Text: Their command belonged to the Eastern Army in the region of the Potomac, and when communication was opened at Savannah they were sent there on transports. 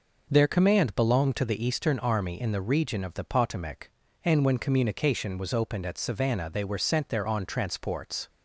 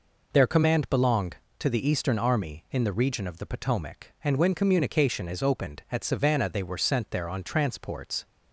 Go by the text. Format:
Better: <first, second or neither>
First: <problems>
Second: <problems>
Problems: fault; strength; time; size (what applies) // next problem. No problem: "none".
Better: first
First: none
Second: says "is" for "was"; at 5.2 s